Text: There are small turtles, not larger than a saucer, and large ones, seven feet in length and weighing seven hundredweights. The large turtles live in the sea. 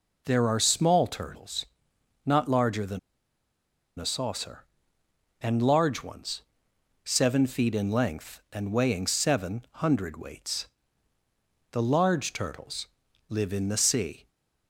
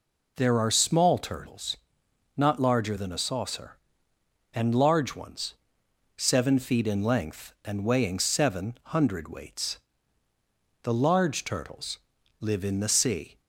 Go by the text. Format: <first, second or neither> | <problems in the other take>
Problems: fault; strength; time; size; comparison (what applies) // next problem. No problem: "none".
second | pauses between "than" and "a"; at 2.9 s; 0.99 s long // pauses between "turtles" and "live"; at 12.8 s; 0.42 s long; also in the second